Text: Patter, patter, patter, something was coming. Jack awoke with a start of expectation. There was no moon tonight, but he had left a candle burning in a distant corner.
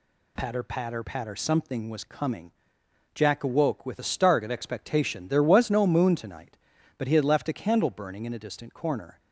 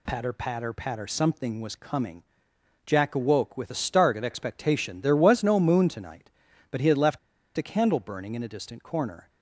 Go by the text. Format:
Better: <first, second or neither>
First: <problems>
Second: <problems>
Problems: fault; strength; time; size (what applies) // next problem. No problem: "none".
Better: first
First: none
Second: pauses between "left" and "a"; at 7.1 s; 0.38 s long